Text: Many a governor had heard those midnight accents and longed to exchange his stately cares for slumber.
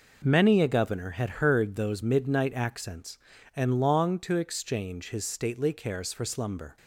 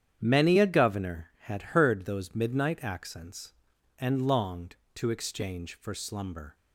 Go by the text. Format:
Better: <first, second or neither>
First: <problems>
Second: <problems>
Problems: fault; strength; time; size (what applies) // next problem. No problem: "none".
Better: first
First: none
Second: starts louder than the rest; strong; until 1.2 s; 9 dB // skips "his stately cares"; at 5.7 s